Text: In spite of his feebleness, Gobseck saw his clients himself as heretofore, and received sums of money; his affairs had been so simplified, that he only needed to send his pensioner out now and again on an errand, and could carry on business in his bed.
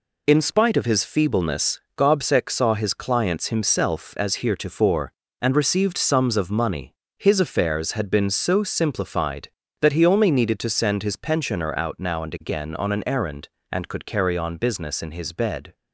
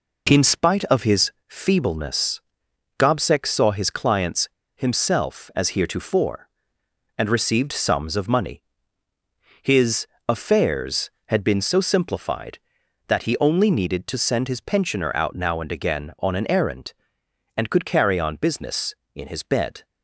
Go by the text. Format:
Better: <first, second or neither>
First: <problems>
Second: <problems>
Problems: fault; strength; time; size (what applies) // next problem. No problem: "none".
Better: first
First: none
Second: pauses between "his" and "feebleness"; slight; at 1.3 s; 0.16 s long // pauses between "clients" and "himself"; slight; at 4.4 s; 0.25 s long // pauses between "his" and "affairs"; slight; at 10.0 s; 0.20 s long